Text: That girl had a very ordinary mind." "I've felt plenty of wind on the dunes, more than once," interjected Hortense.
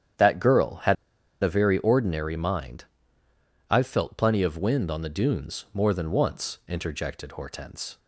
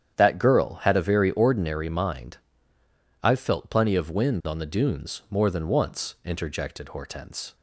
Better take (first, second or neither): second